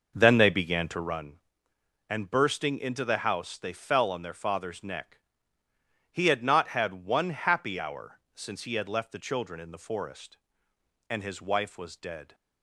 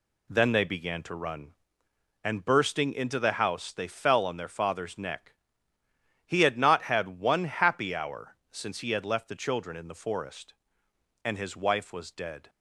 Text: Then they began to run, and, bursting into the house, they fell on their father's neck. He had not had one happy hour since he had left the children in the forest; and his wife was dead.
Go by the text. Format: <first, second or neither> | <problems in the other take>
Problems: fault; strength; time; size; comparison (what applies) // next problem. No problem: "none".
second | starts louder than the rest; noticeable; until 1.3 s; 5.5 dB // pauses between "hour" and "since"; slight; at 8.1 s; 0.16 s long; slight in the second